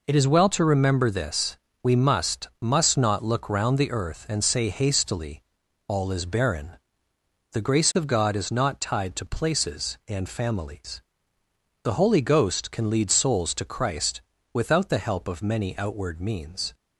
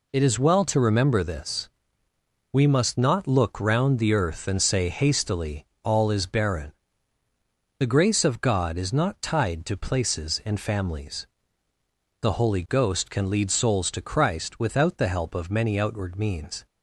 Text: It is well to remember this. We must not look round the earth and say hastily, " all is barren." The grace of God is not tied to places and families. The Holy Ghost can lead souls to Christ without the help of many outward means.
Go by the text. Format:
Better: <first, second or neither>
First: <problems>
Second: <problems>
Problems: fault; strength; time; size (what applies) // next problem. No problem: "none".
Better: second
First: says "must" twice; at 2.6 s // pauses between "Christ" and "without"; slight; at 14.2 s; 0.32 s long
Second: none